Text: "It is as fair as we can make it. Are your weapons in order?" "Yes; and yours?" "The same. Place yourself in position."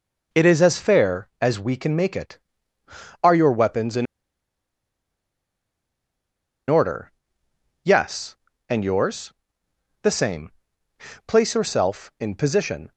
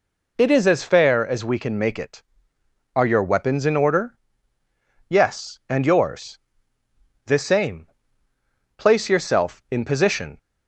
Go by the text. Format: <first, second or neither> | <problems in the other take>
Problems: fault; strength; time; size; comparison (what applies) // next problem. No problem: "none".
second | pauses between "in" and "order"; strong; at 4.0 s; 2.6 s long